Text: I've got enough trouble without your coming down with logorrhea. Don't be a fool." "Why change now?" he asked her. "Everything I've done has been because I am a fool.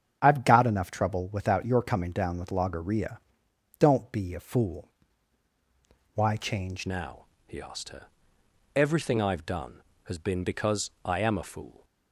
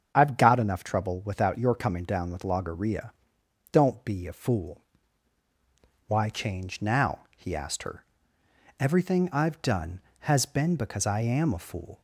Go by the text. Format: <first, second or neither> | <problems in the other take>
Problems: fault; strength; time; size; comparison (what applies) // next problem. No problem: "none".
second | starts louder than the rest; strong; until 1.2 s; 8 dB; also in the second // changes voice at "now"; from 6.8 s on; 5.0 s long